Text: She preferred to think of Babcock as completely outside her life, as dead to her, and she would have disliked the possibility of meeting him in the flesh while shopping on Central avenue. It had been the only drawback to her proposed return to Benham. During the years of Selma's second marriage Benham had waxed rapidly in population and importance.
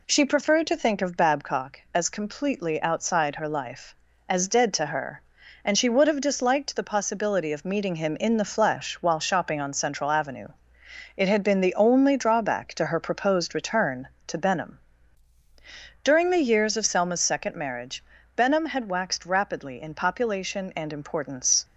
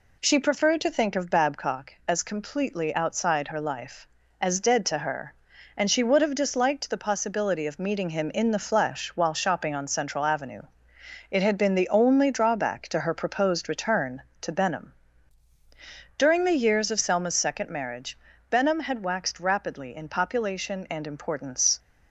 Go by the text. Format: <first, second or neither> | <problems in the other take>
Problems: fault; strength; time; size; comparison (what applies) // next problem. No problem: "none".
neither | pauses between "marriage" and "Benham"; slight; the same in both